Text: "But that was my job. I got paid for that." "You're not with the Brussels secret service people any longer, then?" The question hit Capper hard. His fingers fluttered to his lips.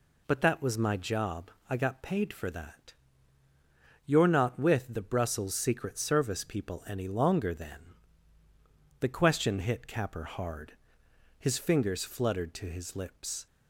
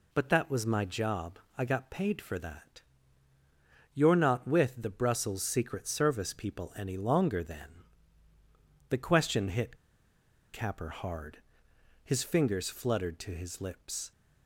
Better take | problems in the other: first | pauses between "hit" and "Capper"; noticeable; at 9.7 s; 0.76 s long

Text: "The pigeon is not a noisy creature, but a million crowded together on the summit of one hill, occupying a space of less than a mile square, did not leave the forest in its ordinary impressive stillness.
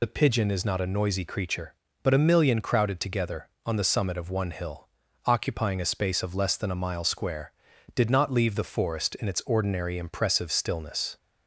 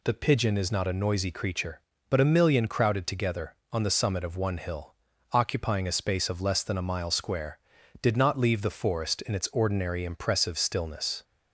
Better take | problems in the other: second | loses the start of "The"; at 0.0 s; 55 ms

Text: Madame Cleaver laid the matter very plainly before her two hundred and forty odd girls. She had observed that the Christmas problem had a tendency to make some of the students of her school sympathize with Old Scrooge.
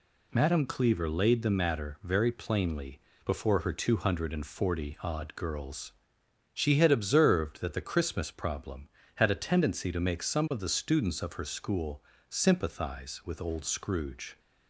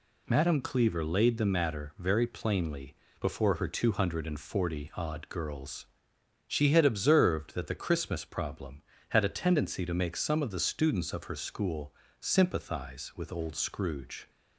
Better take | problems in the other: neither | pauses between "plainly" and "before"; slight; the same in both // pauses between "school" and "sympathize"; slight; the same in both

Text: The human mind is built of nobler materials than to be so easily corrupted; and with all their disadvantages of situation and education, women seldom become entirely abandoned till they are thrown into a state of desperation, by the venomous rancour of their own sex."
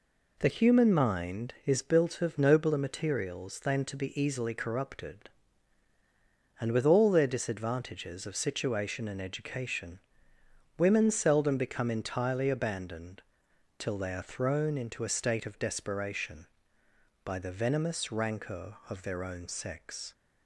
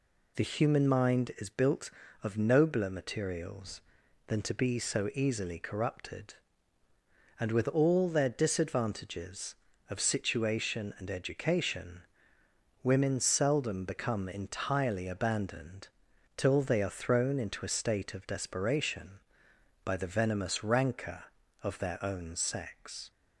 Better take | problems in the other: second | skips "so"; at 4.1 s // pauses between "abandoned" and "till"; noticeable; at 13.2 s; 0.56 s long; noticeable in the second

